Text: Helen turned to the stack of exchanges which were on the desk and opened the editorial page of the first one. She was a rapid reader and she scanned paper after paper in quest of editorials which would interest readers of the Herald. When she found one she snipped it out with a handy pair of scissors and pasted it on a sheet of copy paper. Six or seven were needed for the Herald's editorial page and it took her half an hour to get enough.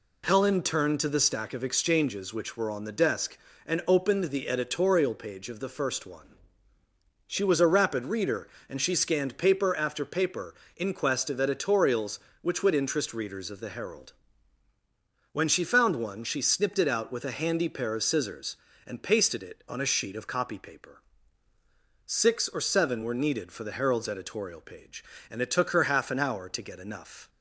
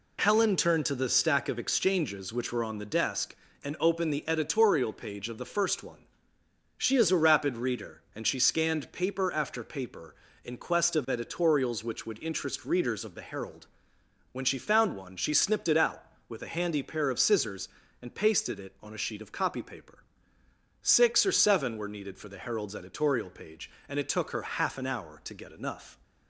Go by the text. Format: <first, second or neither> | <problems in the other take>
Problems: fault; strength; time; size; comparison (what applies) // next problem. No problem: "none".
first | says "is" for "was"; at 6.9 s